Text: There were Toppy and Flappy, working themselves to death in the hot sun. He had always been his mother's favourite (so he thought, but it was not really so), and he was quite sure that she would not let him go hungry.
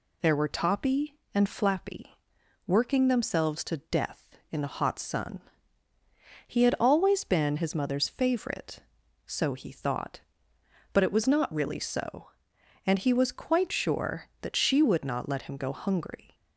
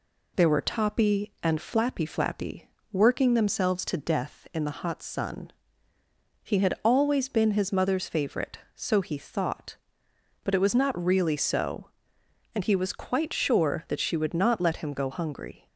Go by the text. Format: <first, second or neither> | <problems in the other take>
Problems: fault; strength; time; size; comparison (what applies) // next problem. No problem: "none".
first | says "Flappy" twice; at 2.0 s